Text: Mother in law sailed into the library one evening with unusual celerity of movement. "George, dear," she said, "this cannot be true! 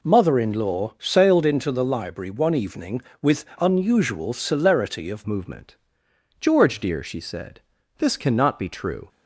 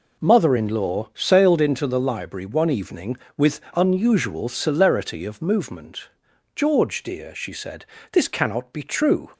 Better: second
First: changes voice at "movement"; from 5.2 s on; 3.8 s long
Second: none

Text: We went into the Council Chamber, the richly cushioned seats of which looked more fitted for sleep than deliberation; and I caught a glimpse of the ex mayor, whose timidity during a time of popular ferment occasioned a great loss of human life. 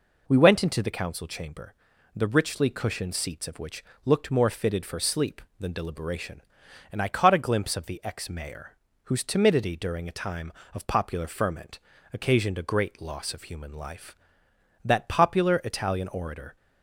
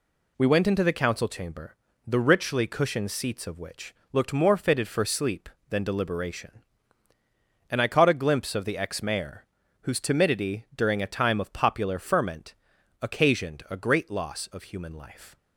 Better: second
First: pauses between "which" and "looked"; slight; at 3.8 s; 0.22 s long // pauses between "ferment" and "occasioned"; slight; at 11.7 s; 0.36 s long // goes on to say "That popular Italian orator"; strong; from 14.8 s on; 1.7 s long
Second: pauses between "which" and "looked"; slight; at 3.9 s; 0.16 s long // pauses between "ferment" and "occasioned"; noticeable; at 12.5 s; 0.46 s long

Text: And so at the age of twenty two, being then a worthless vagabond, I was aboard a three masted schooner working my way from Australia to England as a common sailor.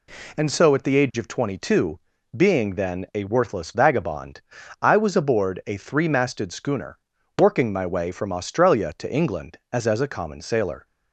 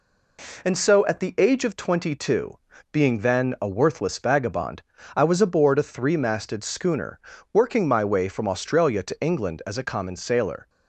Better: second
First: pauses between "schooner" and "working"; at 6.9 s; 0.40 s long // says "as" twice; at 9.8 s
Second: pauses between "schooner" and "working"; slight; at 7.1 s; 0.32 s long

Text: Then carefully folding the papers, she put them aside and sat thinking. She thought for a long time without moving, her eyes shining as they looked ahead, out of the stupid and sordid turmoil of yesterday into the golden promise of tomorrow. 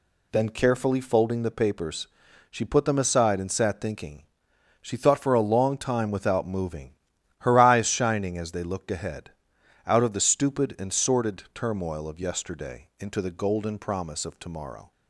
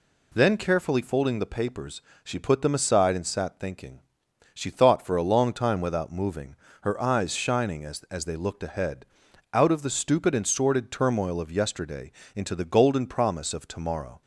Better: first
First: none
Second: says "as" twice; at 8.0 s // pauses between "yesterday" and "into"; slight; at 12.1 s; 0.22 s long

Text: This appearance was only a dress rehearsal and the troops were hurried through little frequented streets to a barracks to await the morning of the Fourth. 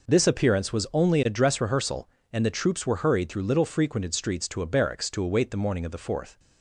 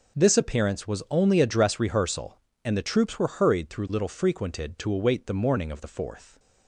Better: first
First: none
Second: skips "streets to a barracks"; at 4.7 s

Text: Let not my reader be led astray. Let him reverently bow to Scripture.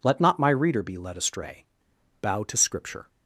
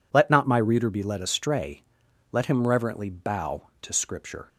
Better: second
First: skips "Let him reverently"; at 1.9 s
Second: none

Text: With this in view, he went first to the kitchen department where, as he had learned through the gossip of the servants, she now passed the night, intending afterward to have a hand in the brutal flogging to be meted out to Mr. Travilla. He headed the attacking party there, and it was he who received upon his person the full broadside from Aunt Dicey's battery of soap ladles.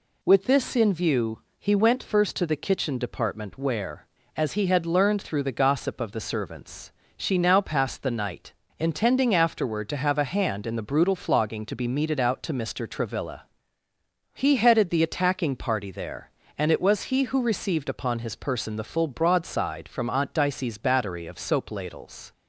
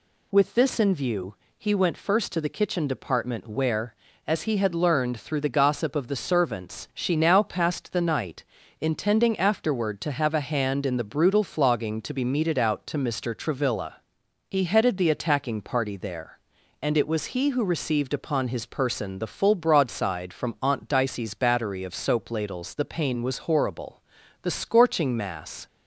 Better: first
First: none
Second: goes on to say "The pain was horrible the scorching mass"; strong; from 22.7 s on; 2.9 s long

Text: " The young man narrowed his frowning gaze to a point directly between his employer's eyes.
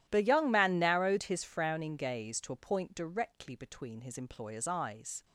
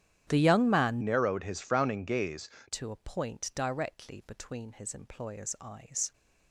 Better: first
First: starts louder than the rest; strong; until 1.0 s; 12 dB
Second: starts louder than the rest; strong; until 1.2 s; 11 dB // changes voice from "narrowed" to "gaze"; from 1.0 to 2.4 s; 1.4 s long

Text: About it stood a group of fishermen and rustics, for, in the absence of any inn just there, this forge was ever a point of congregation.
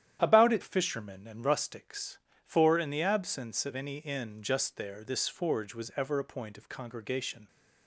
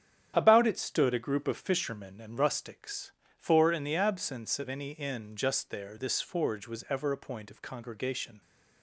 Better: second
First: starts louder than the rest; strong; until 1.2 s; 10.5 dB // skips "stood a group of"; at 0.6 s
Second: starts louder than the rest; strong; until 1.3 s; 9 dB

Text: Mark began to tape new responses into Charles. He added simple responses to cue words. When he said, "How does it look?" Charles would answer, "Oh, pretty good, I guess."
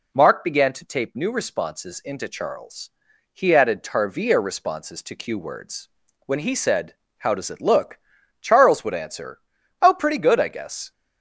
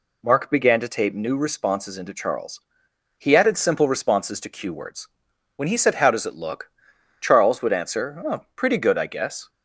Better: second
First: says "tarvia" for "simple"; at 3.8 s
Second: none

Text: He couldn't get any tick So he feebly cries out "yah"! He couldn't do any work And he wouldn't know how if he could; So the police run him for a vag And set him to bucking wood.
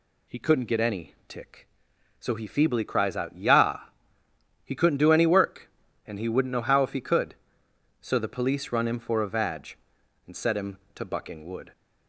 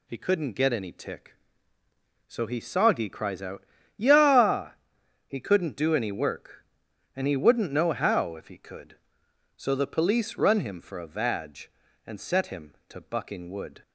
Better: first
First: none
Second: says "soggy" for "feebly"; at 2.5 s // pauses between "out" and "yah"; slight; at 3.6 s; 0.32 s long

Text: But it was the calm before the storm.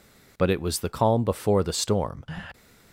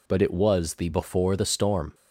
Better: first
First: none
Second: skips "calm"; at 0.8 s

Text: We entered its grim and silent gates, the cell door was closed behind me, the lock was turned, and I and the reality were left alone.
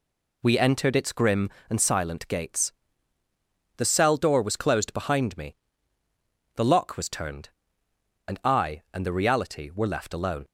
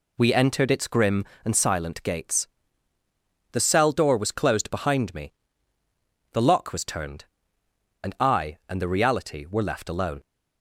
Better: neither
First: none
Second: none

